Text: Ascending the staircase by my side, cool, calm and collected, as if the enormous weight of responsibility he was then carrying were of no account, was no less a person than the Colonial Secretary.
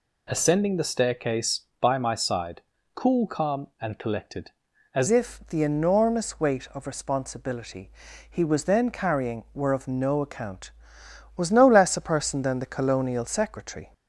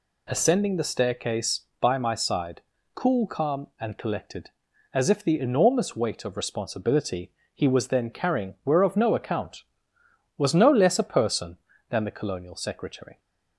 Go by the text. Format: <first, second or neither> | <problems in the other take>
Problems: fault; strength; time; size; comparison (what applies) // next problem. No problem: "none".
second | changes voice at "if"; from 5.0 s on; 8.9 s long // pauses between "responsibility" and "he"; at 7.8 s; 0.40 s long; slight in the second